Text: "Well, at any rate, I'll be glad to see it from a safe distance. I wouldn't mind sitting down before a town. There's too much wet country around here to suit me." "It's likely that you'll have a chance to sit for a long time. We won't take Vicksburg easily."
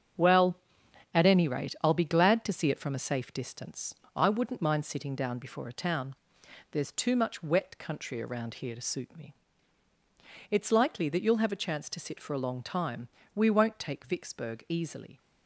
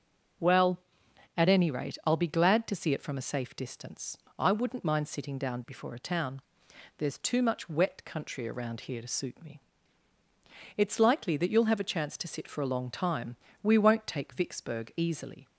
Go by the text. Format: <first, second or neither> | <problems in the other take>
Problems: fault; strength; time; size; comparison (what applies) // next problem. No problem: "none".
second | gets quieter; strong; throughout; 8 dB // starts louder than the rest; strong; until 1.7 s; 7 dB; noticeable in the second